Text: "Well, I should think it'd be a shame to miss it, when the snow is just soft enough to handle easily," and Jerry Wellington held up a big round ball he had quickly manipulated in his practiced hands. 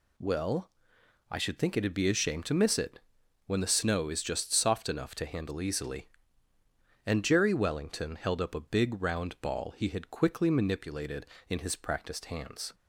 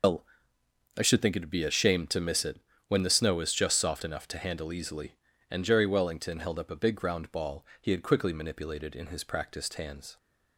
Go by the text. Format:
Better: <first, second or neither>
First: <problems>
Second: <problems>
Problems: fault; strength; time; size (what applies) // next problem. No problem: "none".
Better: first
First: none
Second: loses the start of "Well"; at 0.0 s; 155 ms // pauses between "ball" and "he"; slight; at 7.6 s; 0.16 s long